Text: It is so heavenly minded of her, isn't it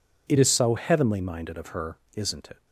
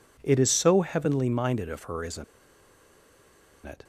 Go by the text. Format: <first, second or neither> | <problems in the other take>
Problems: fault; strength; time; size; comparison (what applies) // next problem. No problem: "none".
first | pauses between "isn't" and "it"; strong; at 2.2 s; 1.4 s long